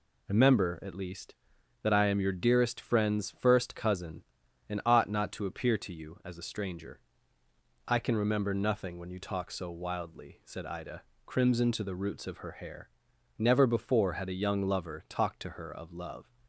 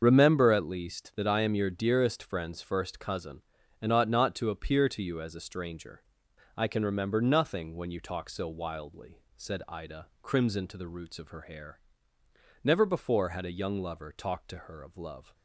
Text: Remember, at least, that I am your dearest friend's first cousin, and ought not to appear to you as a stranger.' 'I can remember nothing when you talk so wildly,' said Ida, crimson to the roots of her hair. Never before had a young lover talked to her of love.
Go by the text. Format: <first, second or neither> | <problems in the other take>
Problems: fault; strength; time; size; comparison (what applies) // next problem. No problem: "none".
first | loses the start of "Remember"; at 0.0 s; 40 ms // starts louder than the rest; until 1.0 s; 6.5 dB